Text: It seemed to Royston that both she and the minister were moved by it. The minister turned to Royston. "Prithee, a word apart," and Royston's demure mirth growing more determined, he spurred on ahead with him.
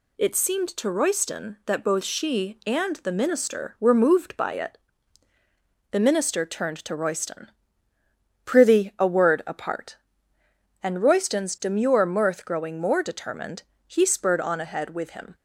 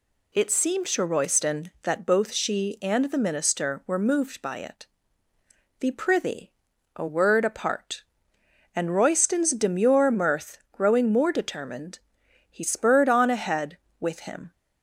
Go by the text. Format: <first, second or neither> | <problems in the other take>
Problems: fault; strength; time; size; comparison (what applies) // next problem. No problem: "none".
first | skips "minister turned to Royston"; at 5.9 s